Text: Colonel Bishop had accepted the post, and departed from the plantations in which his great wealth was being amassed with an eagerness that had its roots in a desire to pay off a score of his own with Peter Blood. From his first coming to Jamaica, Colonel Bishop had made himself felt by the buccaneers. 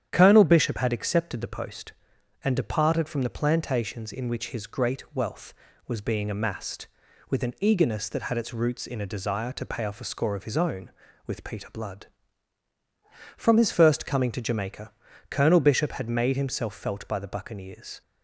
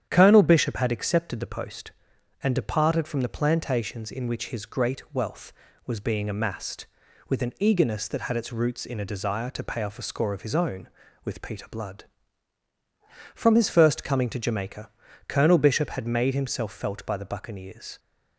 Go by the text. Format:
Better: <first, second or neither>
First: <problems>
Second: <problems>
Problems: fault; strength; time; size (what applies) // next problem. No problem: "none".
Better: neither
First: starts louder than the rest; strong; until 1.1 s; 9.5 dB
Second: starts louder than the rest; strong; until 1.1 s; 9.5 dB